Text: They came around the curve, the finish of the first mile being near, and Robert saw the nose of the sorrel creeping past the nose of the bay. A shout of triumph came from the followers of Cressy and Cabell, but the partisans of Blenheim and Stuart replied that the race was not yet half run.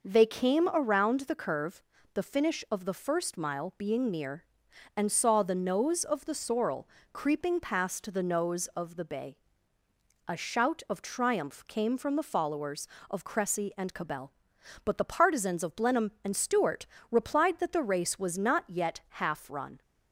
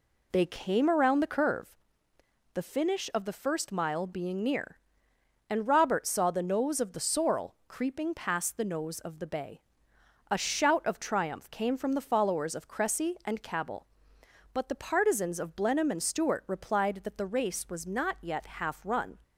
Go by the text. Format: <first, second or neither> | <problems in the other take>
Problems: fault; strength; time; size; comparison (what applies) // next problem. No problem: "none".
second | skips "Robert"; at 5.1 s // pauses between "sorrel" and "creeping"; slight; at 6.8 s; 0.24 s long // pauses between "Stuart" and "replied"; slight; at 16.8 s; 0.26 s long